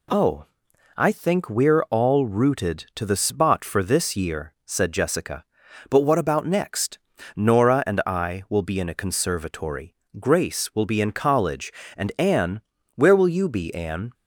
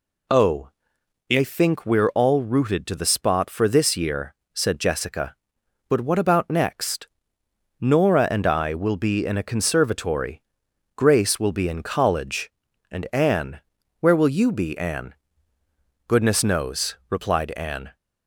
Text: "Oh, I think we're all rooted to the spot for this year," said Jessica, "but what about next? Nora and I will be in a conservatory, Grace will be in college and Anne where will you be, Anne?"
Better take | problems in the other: first | pauses between "Anne" and "where"; at 13.5 s; 0.40 s long; slight in the first // goes on to say "Goodness knows replied Anne"; strong; from 16.0 s on; 1.8 s long

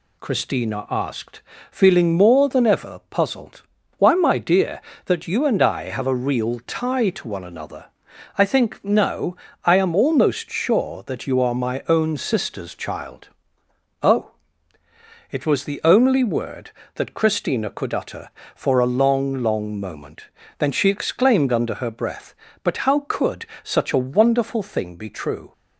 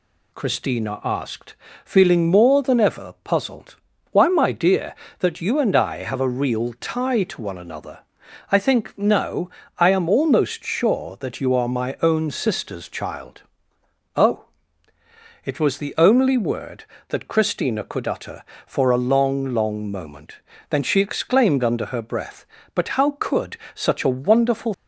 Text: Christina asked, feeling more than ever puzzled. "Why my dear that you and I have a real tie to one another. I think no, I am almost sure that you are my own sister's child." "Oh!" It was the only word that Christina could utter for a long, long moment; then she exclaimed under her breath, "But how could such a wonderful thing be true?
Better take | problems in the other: first | pauses between "could" and "such"; slight; at 23.5 s; 0.18 s long; slight in the first // stops before "thing be true"; at 24.7 s

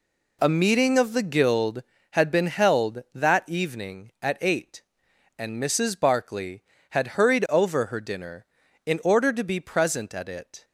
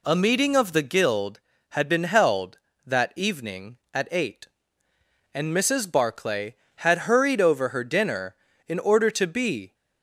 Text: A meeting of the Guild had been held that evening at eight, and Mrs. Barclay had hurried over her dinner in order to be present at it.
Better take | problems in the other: first | stops before "present at it"; at 9.7 s

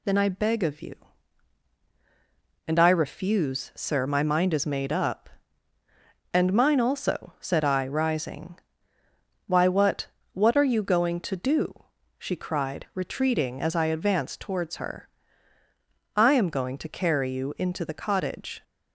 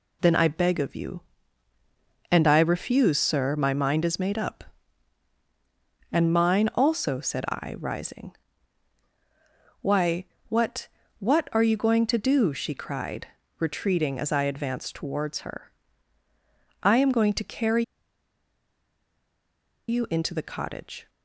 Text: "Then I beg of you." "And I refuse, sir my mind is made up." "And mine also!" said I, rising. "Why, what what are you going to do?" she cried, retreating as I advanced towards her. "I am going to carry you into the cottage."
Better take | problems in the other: first | pauses between "what" and "what"; slight; at 10.8 s; 0.30 s long; slight in the first // pauses between "carry" and "you"; strong; at 17.8 s; 2.0 s long

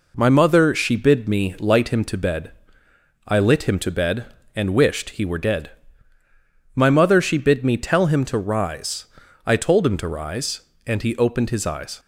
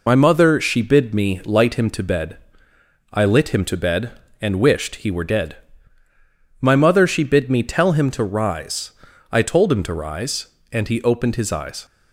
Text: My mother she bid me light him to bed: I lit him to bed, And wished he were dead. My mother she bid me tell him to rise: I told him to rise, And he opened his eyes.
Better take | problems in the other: first | loses the start of "My"; at 0.0 s; 60 ms

